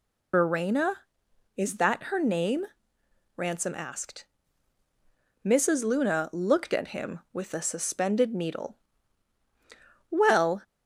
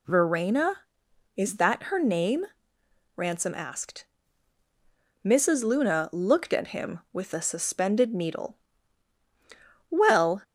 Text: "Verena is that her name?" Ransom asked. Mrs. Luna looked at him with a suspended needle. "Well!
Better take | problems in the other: second | loses the start of "Verena"; at 0.3 s; 65 ms

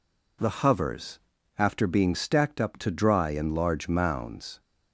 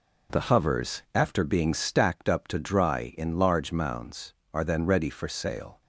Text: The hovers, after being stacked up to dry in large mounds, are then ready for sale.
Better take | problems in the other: second | stops before "are then ready for sale"; at 4.5 s

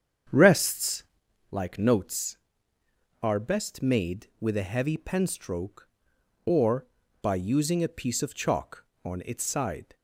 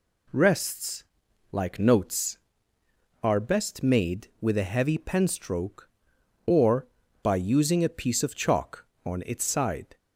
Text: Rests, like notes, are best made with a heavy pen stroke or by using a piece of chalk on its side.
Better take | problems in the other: second | starts louder than the rest; strong; until 1.2 s; 8 dB

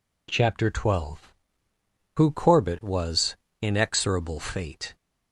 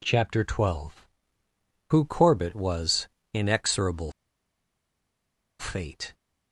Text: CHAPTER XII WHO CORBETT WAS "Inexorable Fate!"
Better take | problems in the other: first | pauses between "WAS" and "Inexorable"; slight; at 3.0 s; 0.26 s long; slight in the first // pauses between "Inexorable" and "Fate"; strong; at 4.1 s; 1.4 s long

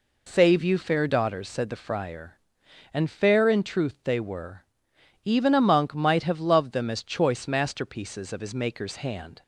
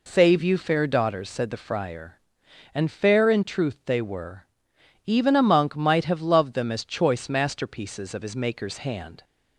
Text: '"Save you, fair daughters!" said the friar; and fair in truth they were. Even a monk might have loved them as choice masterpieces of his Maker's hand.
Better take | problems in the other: neither | none

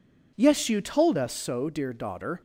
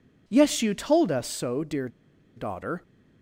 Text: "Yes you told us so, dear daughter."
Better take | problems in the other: first | pauses between "dear" and "daughter"; noticeable; at 1.8 s; 0.48 s long

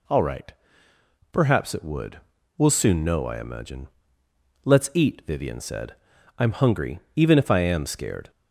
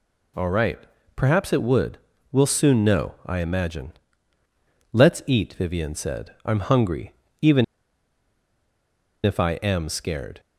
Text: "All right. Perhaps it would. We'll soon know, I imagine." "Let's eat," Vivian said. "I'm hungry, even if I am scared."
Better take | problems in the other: first | pauses between "even" and "if"; strong; at 7.6 s; 1.5 s long

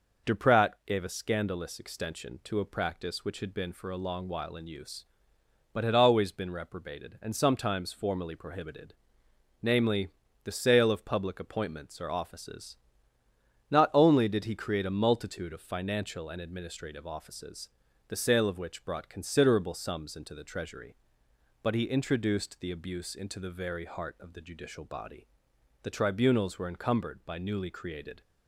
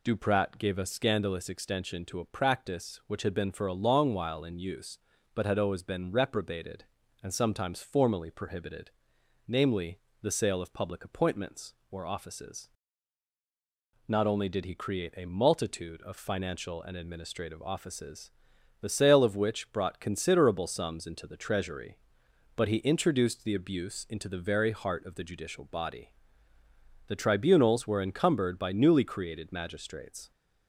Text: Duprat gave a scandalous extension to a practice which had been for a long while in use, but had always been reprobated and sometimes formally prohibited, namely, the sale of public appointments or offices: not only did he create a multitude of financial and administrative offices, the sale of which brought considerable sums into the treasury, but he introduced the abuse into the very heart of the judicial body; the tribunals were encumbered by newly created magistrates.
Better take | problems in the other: second | pauses between "Duprat" and "gave"; slight; at 0.7 s; 0.16 s long // stops before "magistrates"; at 28.2 s

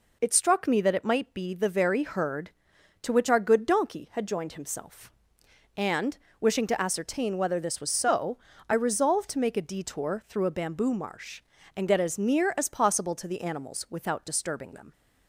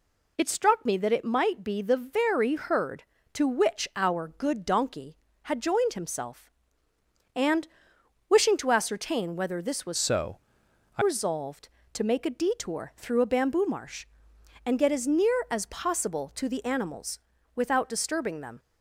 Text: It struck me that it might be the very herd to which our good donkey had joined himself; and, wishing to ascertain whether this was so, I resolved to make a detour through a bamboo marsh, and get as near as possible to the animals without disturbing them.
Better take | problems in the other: first | changes voice from "so" to "I"; from 9.9 to 11.0 s; 1.1 s long // pauses between "animals" and "without"; slight; at 17.1 s; 0.36 s long

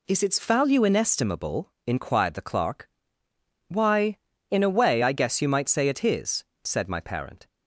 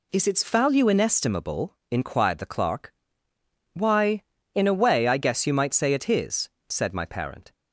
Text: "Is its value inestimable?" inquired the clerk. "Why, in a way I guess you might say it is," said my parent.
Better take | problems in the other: neither | none

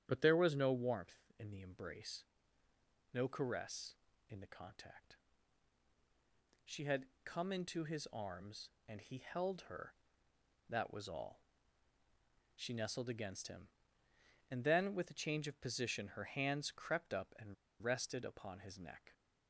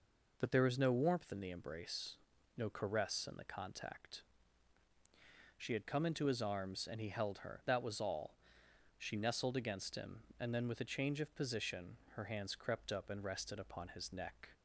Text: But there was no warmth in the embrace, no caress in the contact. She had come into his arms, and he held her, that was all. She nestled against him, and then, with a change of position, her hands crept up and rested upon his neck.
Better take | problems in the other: second | starts louder than the rest; strong; until 1.0 s; 9.5 dB // pauses between "had" and "come"; slight; at 7.0 s; 0.18 s long // pauses between "and" and "rested"; slight; at 17.5 s; 0.27 s long

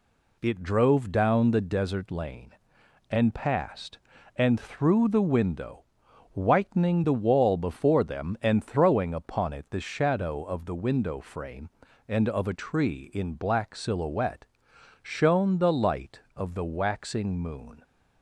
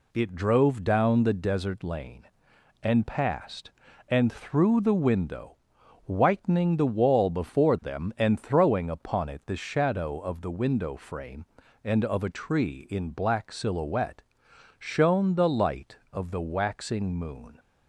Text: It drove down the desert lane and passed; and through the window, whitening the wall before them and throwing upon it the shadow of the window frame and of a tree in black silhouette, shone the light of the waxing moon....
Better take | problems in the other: neither | none

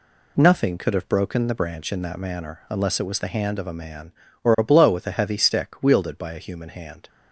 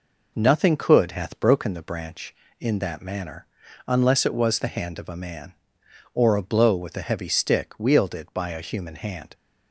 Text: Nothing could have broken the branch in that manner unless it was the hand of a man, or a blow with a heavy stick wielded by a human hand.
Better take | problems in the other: first | says "hath" for "have"; at 1.1 s // pauses between "manner" and "unless"; at 3.4 s; 0.40 s long

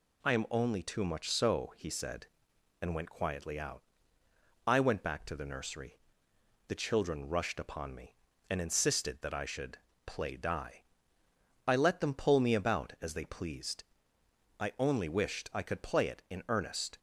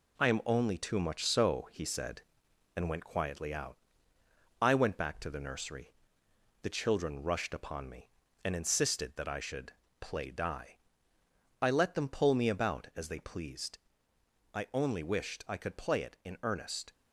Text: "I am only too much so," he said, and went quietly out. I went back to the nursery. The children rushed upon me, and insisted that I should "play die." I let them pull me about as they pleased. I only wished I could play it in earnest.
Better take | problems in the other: first | gets quieter; noticeable; throughout; 5.5 dB // pauses between "should" and "play"; slight; at 9.7 s; 0.28 s long; slight in the first

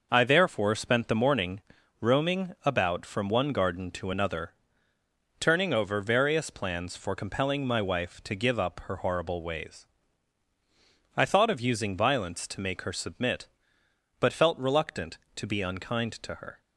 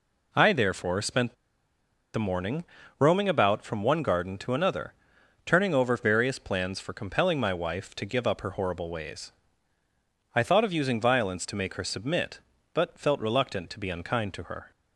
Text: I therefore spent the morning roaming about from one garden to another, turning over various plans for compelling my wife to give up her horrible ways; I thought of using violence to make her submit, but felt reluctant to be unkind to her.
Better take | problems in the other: first | pauses between "spent" and "the"; noticeable; at 1.3 s; 0.80 s long // pauses between "morning" and "roaming"; at 2.6 s; 0.38 s long; also in the first

